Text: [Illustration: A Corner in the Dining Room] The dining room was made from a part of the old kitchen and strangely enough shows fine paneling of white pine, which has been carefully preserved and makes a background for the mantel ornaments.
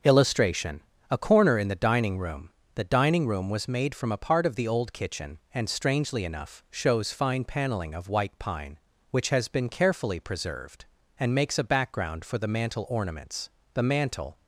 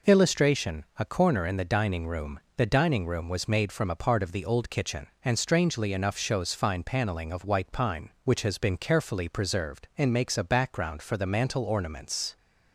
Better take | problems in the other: second | starts louder than the rest; until 1.3 s; 6.5 dB // pauses between "Room" and "The"; slight; at 2.4 s; 0.24 s long; slight in the second // goes on to say "The mantel"; noticeable; from 13.7 s on; 0.64 s long

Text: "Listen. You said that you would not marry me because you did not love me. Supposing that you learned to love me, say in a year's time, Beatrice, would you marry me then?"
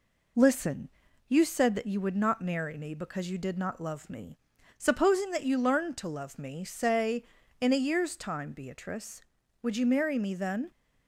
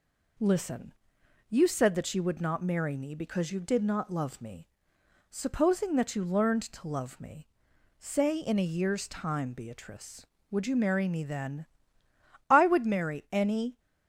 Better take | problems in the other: first | goes on to say "I would marry any"; noticeable; from 12.5 s on; 1.2 s long

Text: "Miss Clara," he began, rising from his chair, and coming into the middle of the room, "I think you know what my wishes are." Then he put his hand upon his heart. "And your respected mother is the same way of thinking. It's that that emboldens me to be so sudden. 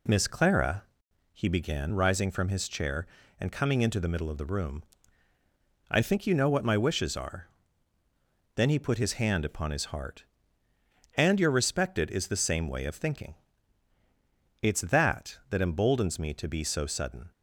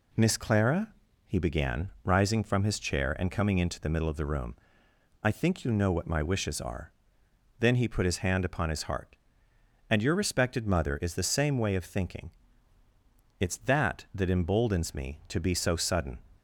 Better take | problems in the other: second | skips "mother"; at 12.0 s

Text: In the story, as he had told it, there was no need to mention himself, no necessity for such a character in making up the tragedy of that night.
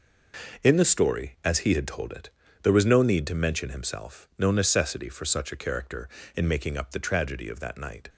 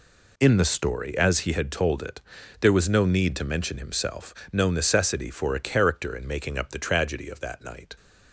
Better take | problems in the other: first | skips "such"; at 5.5 s

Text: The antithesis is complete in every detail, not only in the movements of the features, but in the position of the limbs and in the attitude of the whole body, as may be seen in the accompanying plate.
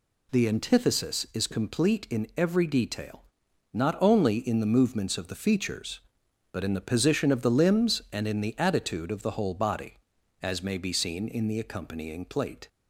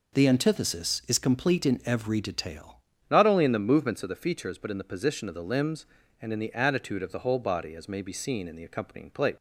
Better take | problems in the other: first | changes voice at "not"; from 3.1 s on; 6.2 s long

